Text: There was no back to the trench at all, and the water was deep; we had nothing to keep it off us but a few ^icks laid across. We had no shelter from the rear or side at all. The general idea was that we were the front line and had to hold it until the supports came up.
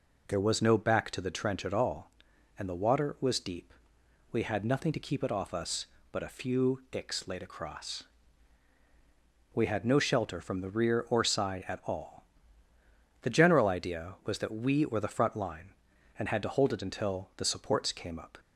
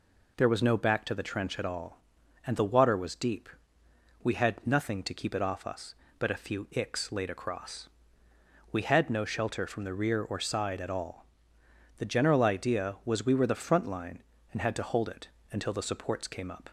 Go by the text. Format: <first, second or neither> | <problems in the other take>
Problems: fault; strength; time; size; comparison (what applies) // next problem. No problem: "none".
first | skips "that"; at 13.2 s // pauses between "it" and "until"; slight; at 15.2 s; 0.24 s long